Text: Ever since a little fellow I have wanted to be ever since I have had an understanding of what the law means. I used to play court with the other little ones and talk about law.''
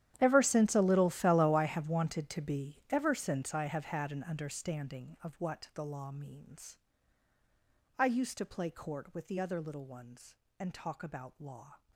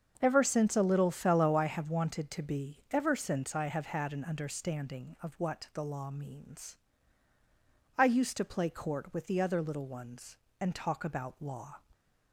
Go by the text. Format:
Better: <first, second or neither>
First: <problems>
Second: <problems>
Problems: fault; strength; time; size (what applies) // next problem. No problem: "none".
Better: second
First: gets quieter; strong; throughout; 18 dB // starts louder than the rest; strong; until 1.2 s; 11 dB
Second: starts louder than the rest; until 1.2 s; 7 dB